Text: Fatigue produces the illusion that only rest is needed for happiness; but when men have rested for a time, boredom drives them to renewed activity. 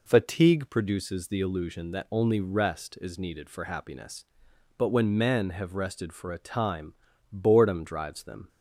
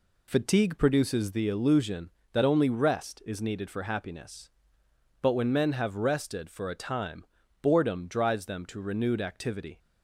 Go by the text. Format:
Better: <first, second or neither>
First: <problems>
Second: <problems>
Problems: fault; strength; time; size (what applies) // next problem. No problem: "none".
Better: second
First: stops before "to renewed activity"; at 8.4 s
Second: none